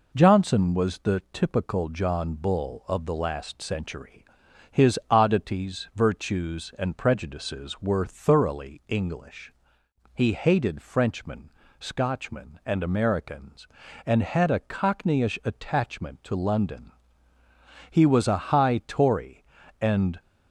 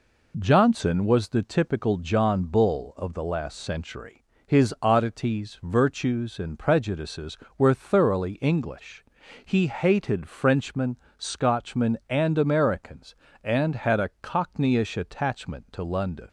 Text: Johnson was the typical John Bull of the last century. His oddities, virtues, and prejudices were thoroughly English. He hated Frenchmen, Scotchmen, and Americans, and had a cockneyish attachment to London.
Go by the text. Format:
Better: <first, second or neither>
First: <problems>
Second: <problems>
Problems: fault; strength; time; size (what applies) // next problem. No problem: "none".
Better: second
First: goes on to say "He was a high Tory and"; strong; from 17.9 s on; 2.2 s long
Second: none